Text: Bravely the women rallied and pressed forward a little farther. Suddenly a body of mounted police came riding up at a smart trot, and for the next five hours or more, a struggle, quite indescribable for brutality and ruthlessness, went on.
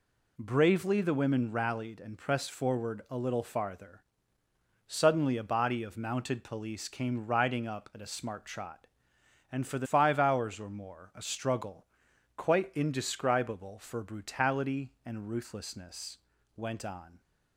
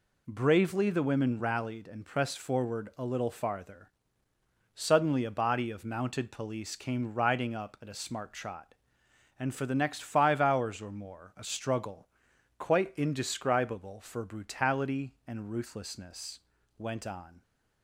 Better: second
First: skips "next"; at 9.8 s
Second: none

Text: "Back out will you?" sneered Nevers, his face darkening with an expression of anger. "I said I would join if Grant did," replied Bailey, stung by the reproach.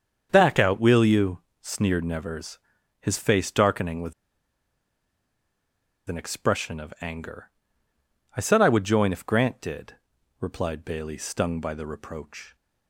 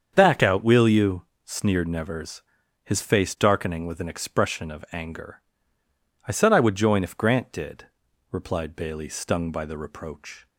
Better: second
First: starts louder than the rest; strong; until 1.3 s; 7.5 dB // pauses between "with" and "an"; strong; at 4.1 s; 1.9 s long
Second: starts louder than the rest; strong; until 1.1 s; 7.5 dB

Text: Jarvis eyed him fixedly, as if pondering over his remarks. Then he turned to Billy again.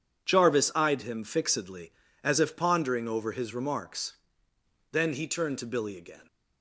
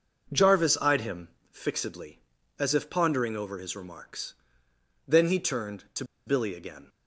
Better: first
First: none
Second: pauses between "him" and "fixedly"; slight; at 1.2 s; 0.22 s long // pauses between "to" and "Billy"; slight; at 6.0 s; 0.22 s long

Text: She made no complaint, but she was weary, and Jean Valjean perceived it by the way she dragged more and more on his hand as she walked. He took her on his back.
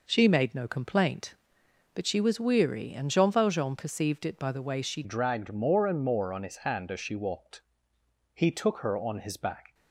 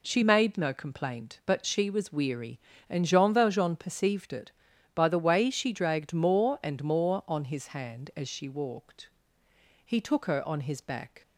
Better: second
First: changes voice at "dragged"; from 5.0 s on; 4.7 s long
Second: none

